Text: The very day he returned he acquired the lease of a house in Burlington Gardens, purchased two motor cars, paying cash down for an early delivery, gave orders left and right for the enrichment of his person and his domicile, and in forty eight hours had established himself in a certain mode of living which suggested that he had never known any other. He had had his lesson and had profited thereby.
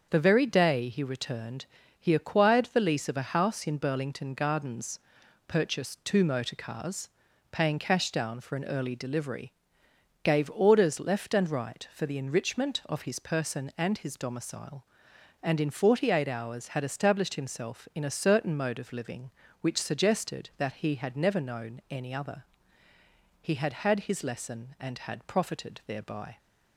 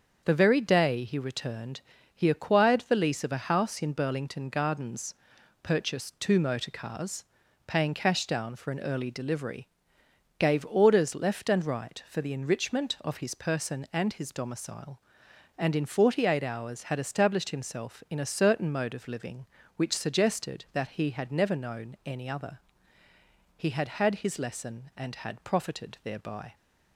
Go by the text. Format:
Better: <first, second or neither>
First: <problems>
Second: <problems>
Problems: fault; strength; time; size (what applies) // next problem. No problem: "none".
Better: neither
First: starts louder than the rest; until 1.1 s; 7 dB // pauses between "returned" and "he"; slight; at 1.6 s; 0.34 s long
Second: starts louder than the rest; until 1.2 s; 6.5 dB // pauses between "returned" and "he"; slight; at 1.8 s; 0.34 s long